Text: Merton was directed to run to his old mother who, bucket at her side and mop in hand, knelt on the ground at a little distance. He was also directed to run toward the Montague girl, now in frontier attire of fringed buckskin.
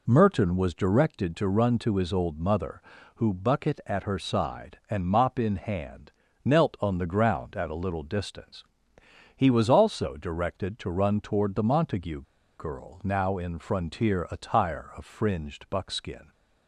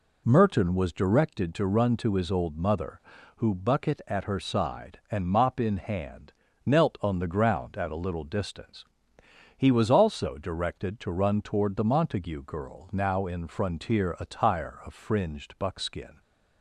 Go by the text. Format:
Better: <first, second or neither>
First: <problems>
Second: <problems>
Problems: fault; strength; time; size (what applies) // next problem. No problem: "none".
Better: second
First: pauses between "Montague" and "girl"; slight; at 12.2 s; 0.35 s long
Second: none